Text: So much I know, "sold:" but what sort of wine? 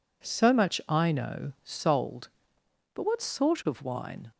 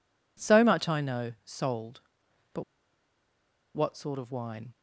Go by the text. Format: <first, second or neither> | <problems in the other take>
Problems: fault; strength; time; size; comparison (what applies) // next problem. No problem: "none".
first | pauses between "but" and "what"; at 2.6 s; 1.1 s long